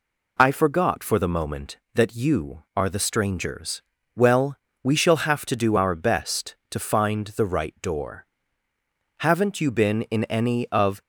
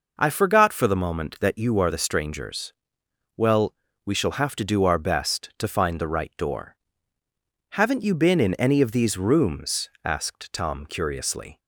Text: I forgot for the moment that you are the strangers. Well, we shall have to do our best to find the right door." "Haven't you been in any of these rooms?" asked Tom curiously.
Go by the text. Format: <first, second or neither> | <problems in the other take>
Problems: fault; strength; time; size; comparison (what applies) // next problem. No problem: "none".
second | stops before "these rooms asked Tom curiously"; at 11.0 s